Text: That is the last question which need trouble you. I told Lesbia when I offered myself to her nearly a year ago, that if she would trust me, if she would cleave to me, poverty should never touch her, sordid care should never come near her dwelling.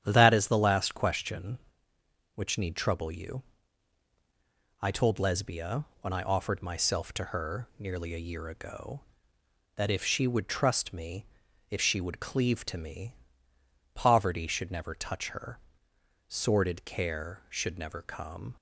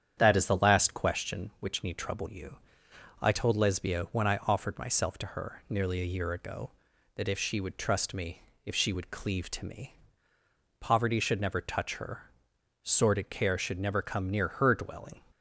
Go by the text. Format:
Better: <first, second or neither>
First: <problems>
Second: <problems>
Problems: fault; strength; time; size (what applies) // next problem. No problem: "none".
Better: second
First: starts louder than the rest; strong; until 1.0 s; 9.5 dB // pauses between "Lesbia" and "when"; slight; at 5.8 s; 0.16 s long // stops before "near her dwelling"; at 18.5 s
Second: starts louder than the rest; strong; until 1.1 s; 9 dB